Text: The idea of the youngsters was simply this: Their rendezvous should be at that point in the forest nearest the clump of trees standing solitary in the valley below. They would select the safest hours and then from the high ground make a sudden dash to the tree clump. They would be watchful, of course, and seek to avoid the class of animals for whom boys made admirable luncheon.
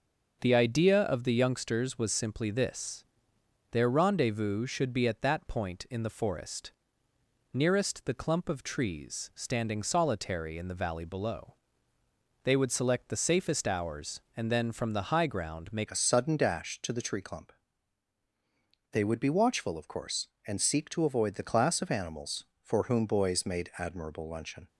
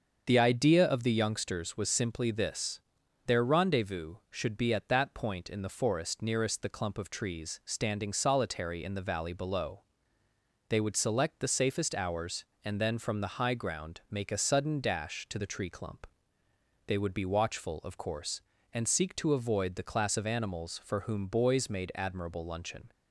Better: second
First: starts louder than the rest; noticeable; until 1.4 s; 6 dB // pauses between "forest" and "nearest"; noticeable; at 6.7 s; 0.82 s long // changes voice at "a"; from 15.8 s on; 8.8 s long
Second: starts louder than the rest; until 1.2 s; 6.5 dB

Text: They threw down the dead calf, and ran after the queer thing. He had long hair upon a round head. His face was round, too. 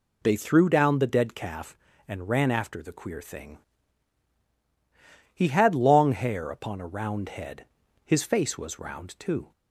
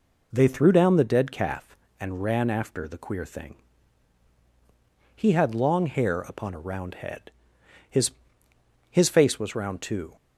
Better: first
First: none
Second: says "His" twice; at 8.9 s

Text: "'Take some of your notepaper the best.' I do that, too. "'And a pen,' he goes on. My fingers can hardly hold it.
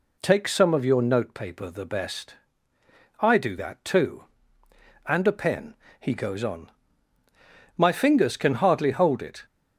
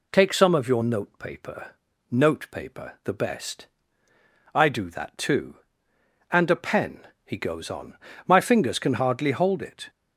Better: first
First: none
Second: says "notepaper" twice; at 2.0 s

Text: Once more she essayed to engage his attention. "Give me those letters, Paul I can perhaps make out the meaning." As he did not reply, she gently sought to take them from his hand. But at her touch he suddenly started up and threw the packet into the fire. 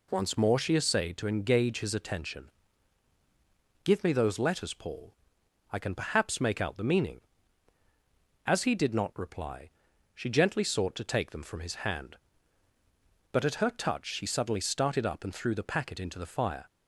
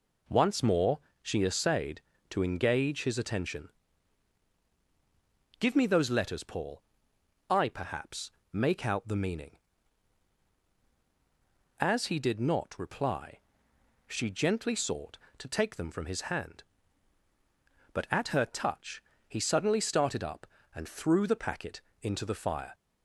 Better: first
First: pauses between "Paul" and "I"; noticeable; at 5.1 s; 0.58 s long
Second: pauses between "more" and "she"; slight; at 0.9 s; 0.22 s long // pauses between "Paul" and "I"; noticeable; at 6.8 s; 0.68 s long // skips "can"; at 7.6 s // pauses between "perhaps" and "make"; slight; at 8.3 s; 0.20 s long // pauses between "touch" and "he"; slight; at 19.0 s; 0.24 s long // pauses between "packet" and "into"; slight; at 21.8 s; 0.20 s long

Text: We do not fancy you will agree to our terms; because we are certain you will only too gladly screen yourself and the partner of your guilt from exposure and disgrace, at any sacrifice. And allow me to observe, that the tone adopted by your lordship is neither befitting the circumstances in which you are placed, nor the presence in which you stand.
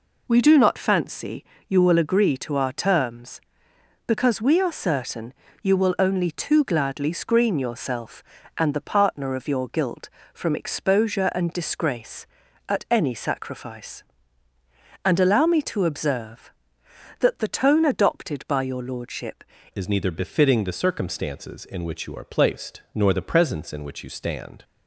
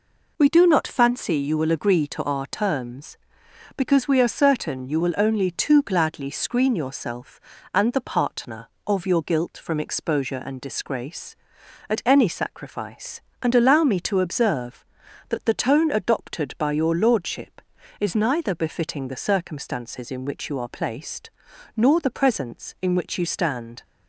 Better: second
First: pauses between "fancy" and "you"; slight; at 1.4 s; 0.24 s long // pauses between "certain" and "you"; slight; at 5.3 s; 0.30 s long // changes voice at "is"; from 19.7 s on; 4.9 s long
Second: none

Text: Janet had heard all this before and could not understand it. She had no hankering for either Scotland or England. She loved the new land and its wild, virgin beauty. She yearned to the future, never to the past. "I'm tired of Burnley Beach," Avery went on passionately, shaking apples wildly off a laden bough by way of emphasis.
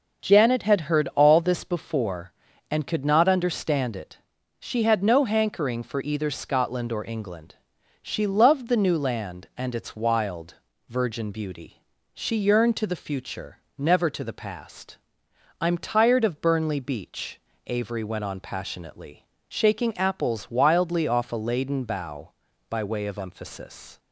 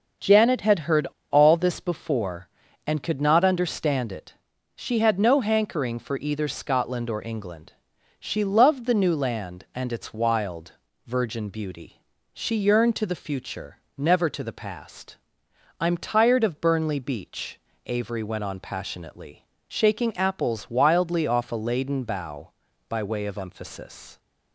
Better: first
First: none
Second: pauses between "heard" and "all"; slight; at 1.0 s; 0.22 s long

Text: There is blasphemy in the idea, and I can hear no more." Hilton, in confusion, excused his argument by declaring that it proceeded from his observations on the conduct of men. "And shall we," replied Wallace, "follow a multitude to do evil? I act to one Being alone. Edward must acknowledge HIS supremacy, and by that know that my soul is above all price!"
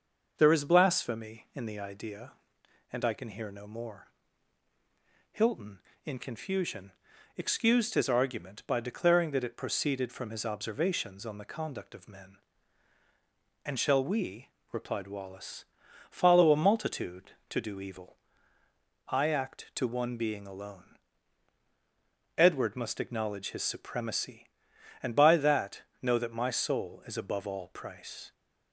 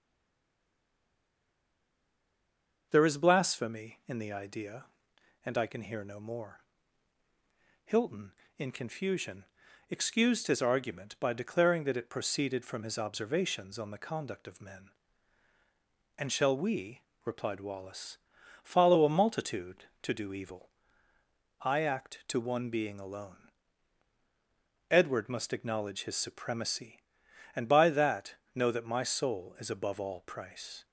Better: first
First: pauses between "that" and "know"; slight; at 25.8 s; 0.20 s long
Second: stays silent before the first word; strong; until 2.9 s; 2.9 s long // pauses between "that" and "know"; slight; at 28.3 s; 0.20 s long

